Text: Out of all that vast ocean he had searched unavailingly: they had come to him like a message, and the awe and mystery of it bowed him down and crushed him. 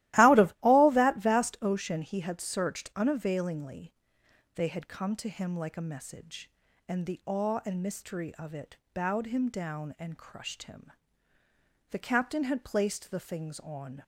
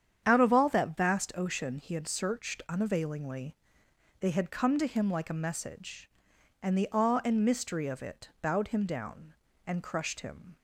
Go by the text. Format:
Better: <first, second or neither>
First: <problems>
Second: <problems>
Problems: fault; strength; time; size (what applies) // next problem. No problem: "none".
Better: second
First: starts louder than the rest; strong; until 1.2 s; 16.5 dB // pauses between "it" and "bowed"; slight; at 8.7 s; 0.16 s long // goes on to say "The captain had placed the things on"; strong; from 11.9 s on; 2.1 s long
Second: starts louder than the rest; strong; until 1.2 s; 8.5 dB